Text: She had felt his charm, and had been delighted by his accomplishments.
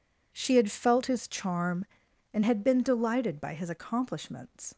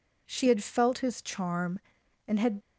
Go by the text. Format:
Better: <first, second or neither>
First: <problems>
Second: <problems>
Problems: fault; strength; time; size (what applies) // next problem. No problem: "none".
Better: first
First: none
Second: stops before "been delighted by his accomplishments"; at 2.6 s